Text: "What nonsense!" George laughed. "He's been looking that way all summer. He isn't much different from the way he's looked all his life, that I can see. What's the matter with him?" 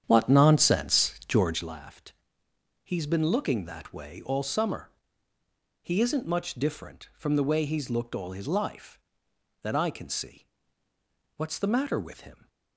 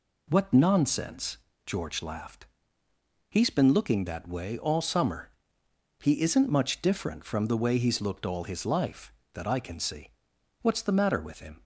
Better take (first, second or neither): second